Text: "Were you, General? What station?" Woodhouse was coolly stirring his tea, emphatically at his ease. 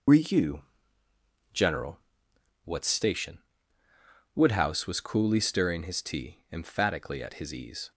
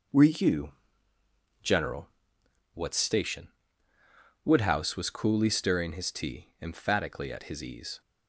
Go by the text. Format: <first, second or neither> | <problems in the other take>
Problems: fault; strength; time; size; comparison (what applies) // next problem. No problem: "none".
second | loses the start of "Were"; at 0.0 s; 70 ms